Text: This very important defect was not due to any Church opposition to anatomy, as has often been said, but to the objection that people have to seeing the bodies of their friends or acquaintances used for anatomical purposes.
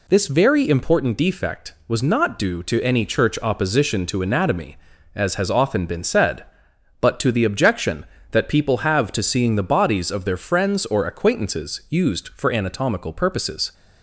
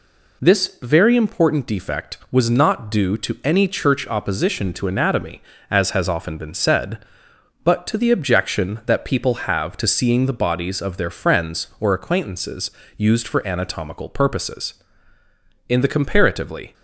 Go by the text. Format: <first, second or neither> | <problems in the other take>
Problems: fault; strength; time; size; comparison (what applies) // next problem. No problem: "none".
first | pauses between "acquaintances" and "used"; slight; at 12.7 s; 0.24 s long // goes on to say "In the comparatively"; noticeable; from 15.6 s on; 1.0 s long